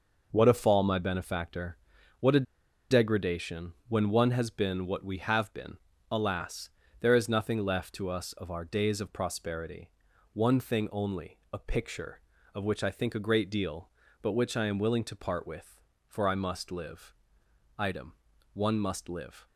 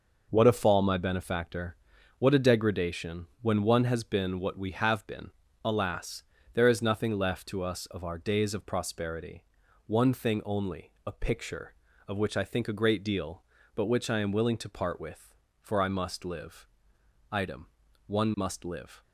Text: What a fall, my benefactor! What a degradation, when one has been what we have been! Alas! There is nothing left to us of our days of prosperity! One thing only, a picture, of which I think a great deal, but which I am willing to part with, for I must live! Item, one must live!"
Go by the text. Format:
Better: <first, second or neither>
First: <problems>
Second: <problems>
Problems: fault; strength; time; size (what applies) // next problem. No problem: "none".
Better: second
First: pauses between "a" and "degradation"; noticeable; at 2.4 s; 0.47 s long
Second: none